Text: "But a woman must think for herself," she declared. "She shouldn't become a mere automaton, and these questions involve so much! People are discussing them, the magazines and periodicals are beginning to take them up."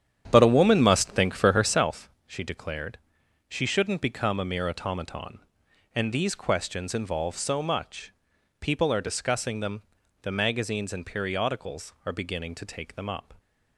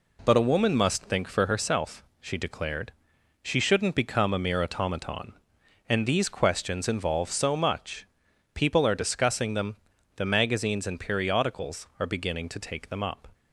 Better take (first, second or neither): second